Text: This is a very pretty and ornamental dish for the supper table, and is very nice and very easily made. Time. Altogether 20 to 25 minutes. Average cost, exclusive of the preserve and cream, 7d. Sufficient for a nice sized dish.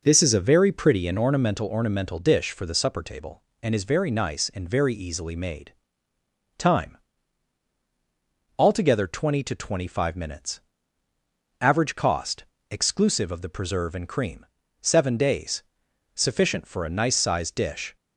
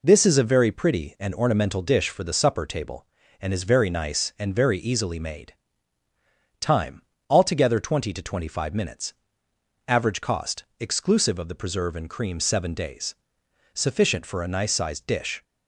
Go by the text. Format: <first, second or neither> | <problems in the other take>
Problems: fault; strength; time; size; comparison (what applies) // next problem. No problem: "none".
second | says "ornamental" twice; at 1.6 s